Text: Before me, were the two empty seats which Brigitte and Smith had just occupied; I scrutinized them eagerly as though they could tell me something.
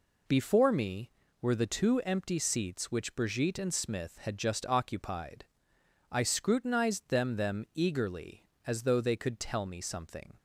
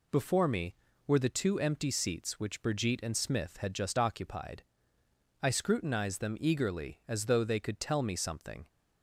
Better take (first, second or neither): second